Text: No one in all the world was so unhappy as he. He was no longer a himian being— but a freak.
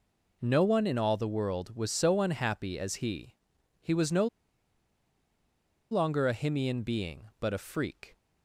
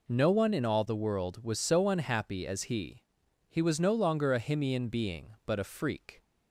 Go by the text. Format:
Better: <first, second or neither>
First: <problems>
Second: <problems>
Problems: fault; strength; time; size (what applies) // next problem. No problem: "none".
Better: second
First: pauses between "no" and "longer"; strong; at 4.2 s; 1.6 s long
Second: none